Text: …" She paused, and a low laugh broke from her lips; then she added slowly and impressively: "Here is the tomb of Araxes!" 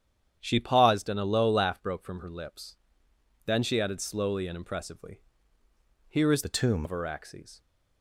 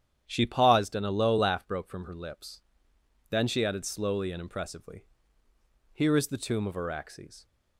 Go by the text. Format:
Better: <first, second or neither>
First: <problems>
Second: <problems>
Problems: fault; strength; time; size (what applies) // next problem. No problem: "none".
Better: second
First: starts louder than the rest; strong; until 1.4 s; 9 dB // changes voice from "the" to "tomb"; from 6.4 to 6.8 s; 0.4 s long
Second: starts louder than the rest; strong; until 1.2 s; 9.5 dB